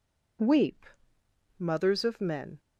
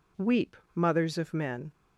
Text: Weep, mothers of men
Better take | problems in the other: neither | none

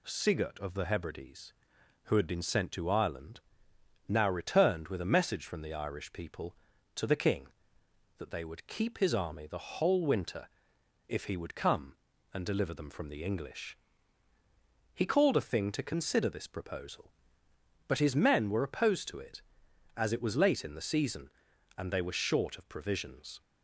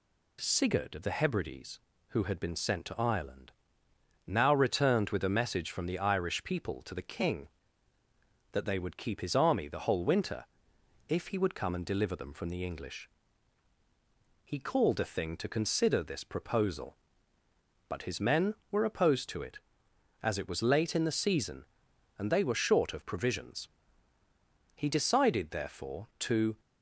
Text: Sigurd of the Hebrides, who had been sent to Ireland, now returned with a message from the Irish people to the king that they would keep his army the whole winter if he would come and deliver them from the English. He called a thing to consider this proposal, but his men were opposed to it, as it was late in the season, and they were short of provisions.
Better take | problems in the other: first | pauses between "winter" and "if"; noticeable; at 10.4 s; 0.62 s long; noticeable in the first // goes on to say "He decided therefore to"; strong; from 24.7 s on; 1.8 s long

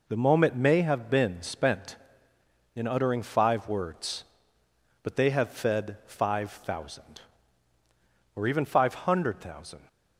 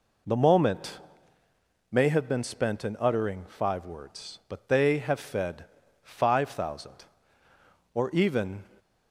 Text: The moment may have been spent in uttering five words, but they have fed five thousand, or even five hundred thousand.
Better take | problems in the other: first | pauses between "moment" and "may"; noticeable; at 0.9 s; 0.94 s long // pauses between "fed" and "five"; at 5.6 s; 0.38 s long // stops before "five hundred thousand"; at 8.7 s

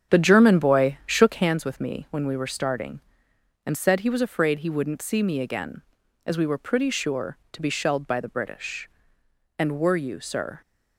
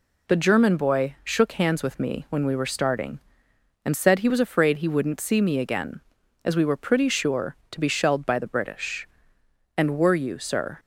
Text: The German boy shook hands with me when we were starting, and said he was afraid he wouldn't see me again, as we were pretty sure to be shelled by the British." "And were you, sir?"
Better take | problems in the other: second | starts louder than the rest; strong; until 1.6 s; 8.5 dB

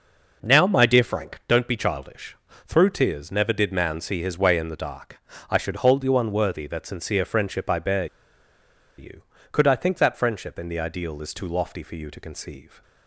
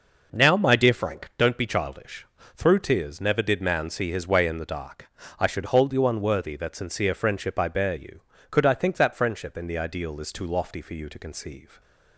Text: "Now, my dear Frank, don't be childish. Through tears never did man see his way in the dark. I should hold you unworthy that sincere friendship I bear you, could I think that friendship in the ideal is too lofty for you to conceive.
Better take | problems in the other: second | pauses between "bear" and "you"; noticeable; at 8.0 s; 0.92 s long

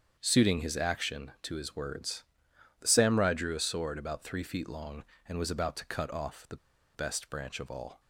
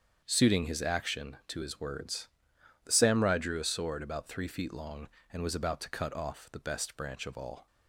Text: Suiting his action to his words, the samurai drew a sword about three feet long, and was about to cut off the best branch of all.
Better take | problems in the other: second | starts louder than the rest; strong; until 1.2 s; 7.5 dB; strong in the second // pauses between "the" and "best"; at 6.5 s; 0.39 s long

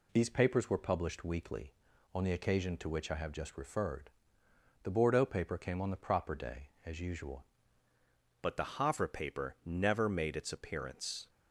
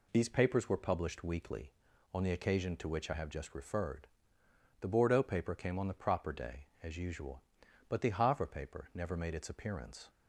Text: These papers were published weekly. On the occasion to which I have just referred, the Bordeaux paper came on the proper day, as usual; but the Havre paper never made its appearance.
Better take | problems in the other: second | changes voice at "but"; from 8.4 s on; 2.8 s long

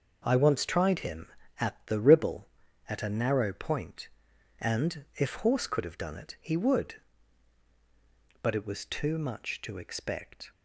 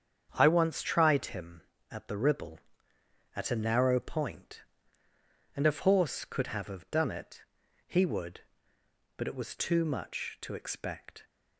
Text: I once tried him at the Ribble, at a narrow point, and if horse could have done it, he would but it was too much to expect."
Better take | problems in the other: first | starts louder than the rest; strong; until 1.3 s; 8 dB // says "have" twice; at 6.6 s

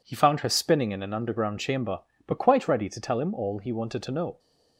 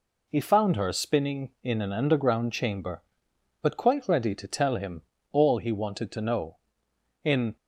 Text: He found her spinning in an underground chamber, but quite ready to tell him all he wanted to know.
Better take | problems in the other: first | pauses between "him" and "all"; slight; at 5.0 s; 0.30 s long // goes on to say "In"; slight; from 7.2 s on; 0.32 s long

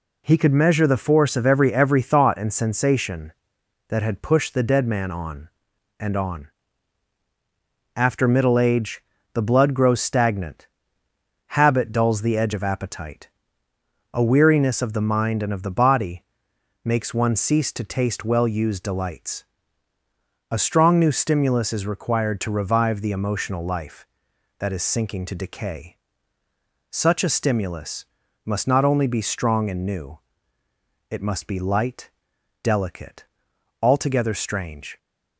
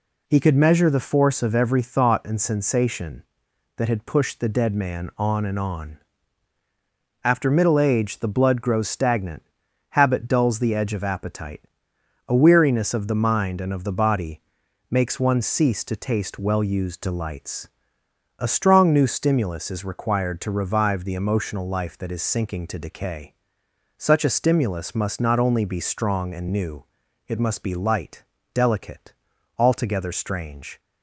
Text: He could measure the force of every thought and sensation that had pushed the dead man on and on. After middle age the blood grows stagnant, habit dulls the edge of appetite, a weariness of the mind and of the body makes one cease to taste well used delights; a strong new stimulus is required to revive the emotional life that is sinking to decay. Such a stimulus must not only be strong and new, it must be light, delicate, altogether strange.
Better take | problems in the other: second | says "every" twice; at 1.7 s // pauses between "age" and "the"; slight; at 9.0 s; 0.32 s long // pauses between "body" and "makes"; noticeable; at 16.2 s; 0.62 s long; noticeable in the second // pauses between "stimulus" and "must"; at 28.0 s; 0.38 s long

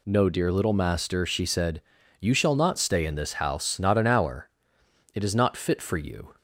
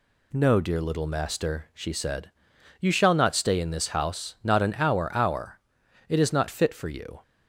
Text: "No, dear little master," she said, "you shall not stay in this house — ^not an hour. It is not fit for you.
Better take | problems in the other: first | says "hour" twice; at 5.1 s

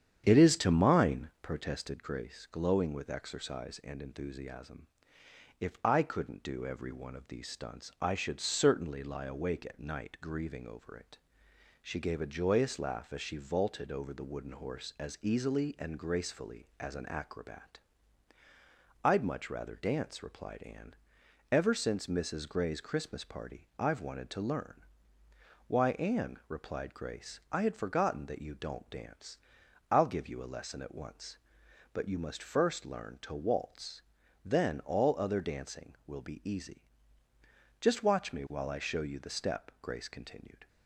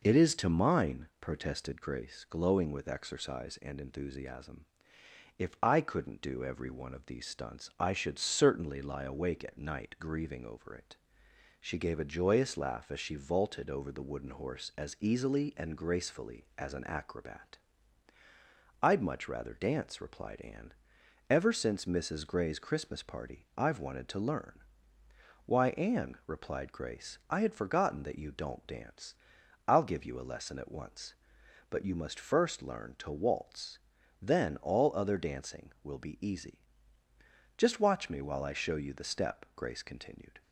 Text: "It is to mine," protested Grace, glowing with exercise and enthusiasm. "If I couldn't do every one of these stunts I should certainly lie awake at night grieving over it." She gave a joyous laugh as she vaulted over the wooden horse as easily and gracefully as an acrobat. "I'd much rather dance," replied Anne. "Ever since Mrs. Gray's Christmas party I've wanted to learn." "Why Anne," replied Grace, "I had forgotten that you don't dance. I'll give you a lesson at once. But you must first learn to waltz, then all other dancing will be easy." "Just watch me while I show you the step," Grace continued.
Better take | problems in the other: second | starts louder than the rest; strong; until 1.6 s; 9 dB

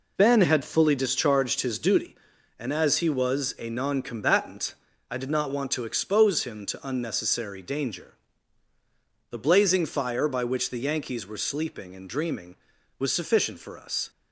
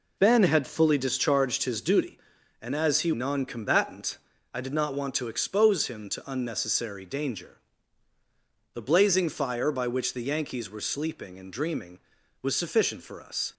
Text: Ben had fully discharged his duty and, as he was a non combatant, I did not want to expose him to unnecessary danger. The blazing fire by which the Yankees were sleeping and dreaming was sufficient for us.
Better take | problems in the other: first | skips "was a"; at 3.1 s

